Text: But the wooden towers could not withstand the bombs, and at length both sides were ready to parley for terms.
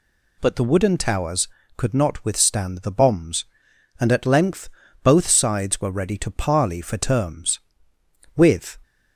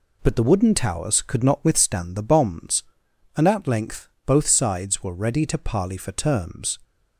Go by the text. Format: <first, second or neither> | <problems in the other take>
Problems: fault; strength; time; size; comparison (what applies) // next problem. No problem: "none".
second | pauses between "length" and "both"; slight; at 4.6 s; 0.34 s long; slight in the second // goes on to say "With"; slight; from 8.3 s on; 0.44 s long